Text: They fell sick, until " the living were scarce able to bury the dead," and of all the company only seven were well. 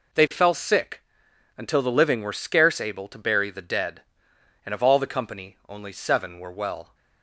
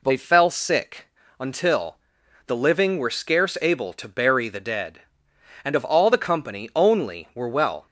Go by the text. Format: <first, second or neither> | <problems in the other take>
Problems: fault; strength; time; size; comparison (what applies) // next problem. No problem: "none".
first | skips "seven"; at 7.3 s